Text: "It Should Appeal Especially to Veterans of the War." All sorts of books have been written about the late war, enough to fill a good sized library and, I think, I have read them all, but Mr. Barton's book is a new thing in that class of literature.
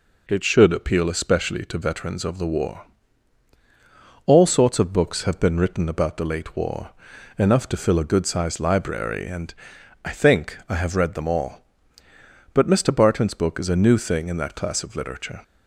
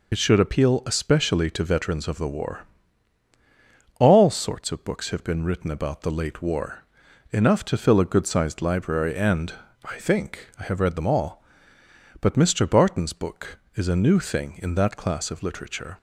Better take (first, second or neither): first